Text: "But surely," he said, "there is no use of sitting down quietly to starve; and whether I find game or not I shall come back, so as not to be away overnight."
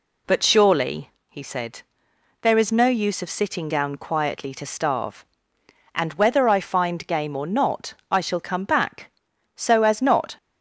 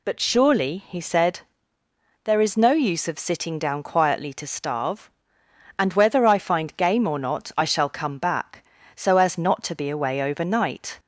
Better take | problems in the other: second | stops before "to be away overnight"; at 10.3 s

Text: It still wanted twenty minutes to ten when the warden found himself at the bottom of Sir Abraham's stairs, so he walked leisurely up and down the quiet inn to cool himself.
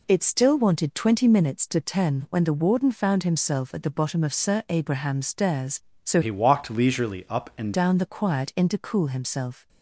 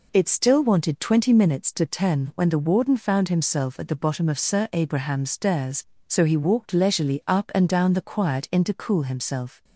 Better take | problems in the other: second | changes voice from "he" to "and"; from 6.2 to 7.7 s; 1.5 s long

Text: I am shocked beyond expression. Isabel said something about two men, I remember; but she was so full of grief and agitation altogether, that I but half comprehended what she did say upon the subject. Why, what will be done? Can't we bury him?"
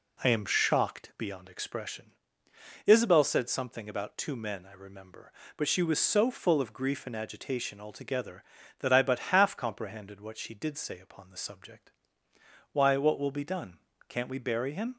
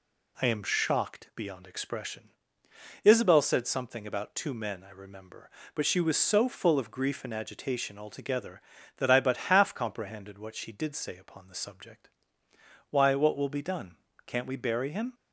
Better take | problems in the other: second | starts louder than the rest; slight; until 1.4 s; 2.5 dB

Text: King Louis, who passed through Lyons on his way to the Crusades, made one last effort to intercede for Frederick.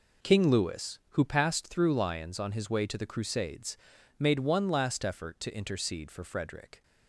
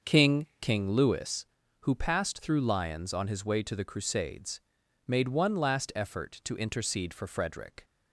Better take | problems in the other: first | starts louder than the rest; until 1.1 s; 6.5 dB // says "King" twice; at 0.5 s

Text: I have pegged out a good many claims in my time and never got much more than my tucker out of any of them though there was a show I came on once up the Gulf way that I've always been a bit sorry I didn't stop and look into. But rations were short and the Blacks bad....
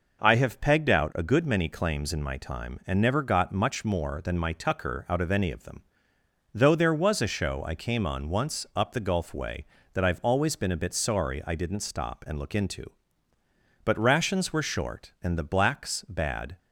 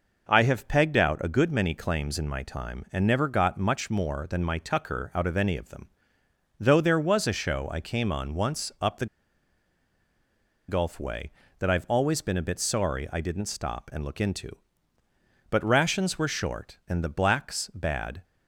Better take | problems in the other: first | pauses between "them" and "though"; noticeable; at 5.8 s; 0.72 s long; noticeable in the first // pauses between "the" and "Gulf"; strong; at 9.0 s; 1.6 s long

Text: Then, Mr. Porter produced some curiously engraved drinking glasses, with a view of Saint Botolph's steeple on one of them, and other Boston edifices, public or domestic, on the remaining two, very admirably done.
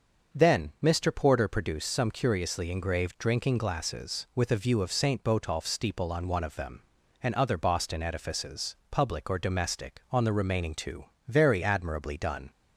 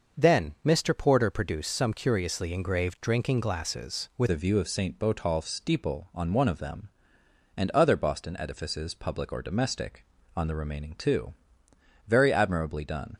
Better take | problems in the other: first | starts louder than the rest; noticeable; until 1.2 s; 6 dB; also in the first // changes voice at "a"; from 4.2 s on; 8.9 s long

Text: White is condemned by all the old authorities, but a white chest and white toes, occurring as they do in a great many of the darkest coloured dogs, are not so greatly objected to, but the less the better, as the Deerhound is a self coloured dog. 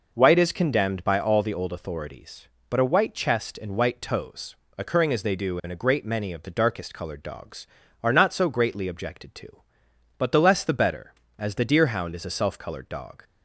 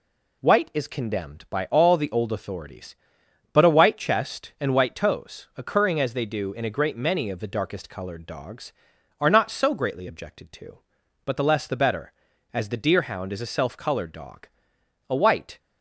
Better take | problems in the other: first | goes on to say "A white"; from 15.0 s on; 0.50 s long

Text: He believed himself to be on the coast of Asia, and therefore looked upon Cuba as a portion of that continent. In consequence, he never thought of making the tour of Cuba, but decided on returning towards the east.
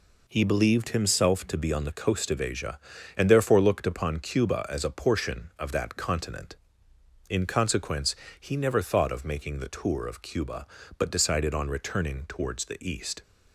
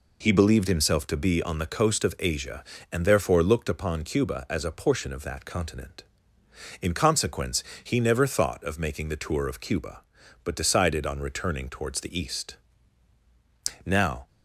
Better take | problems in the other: first | goes on to say "Now"; slight; from 13.8 s on; 0.44 s long

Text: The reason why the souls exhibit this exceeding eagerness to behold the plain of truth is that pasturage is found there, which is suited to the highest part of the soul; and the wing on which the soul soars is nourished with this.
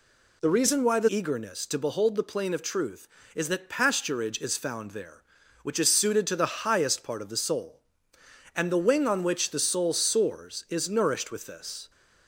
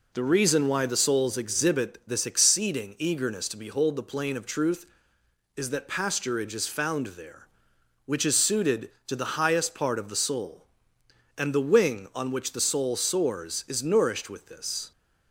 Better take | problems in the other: second | skips "souls exhibit this exceeding"; at 1.0 s

